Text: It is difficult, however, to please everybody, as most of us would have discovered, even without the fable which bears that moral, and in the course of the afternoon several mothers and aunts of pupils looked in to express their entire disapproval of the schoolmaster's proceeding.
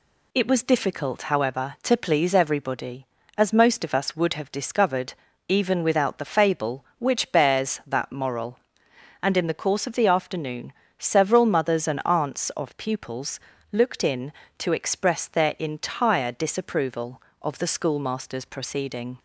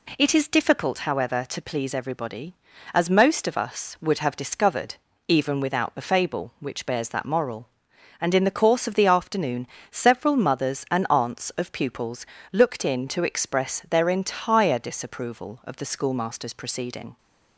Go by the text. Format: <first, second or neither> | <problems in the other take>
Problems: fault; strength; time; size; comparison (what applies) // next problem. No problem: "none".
second | says "was" for "is"; at 0.4 s // pauses between "afternoon" and "several"; slight; at 10.7 s; 0.28 s long; slight in the second // pauses between "pupils" and "looked"; slight; at 13.4 s; 0.32 s long; slight in the second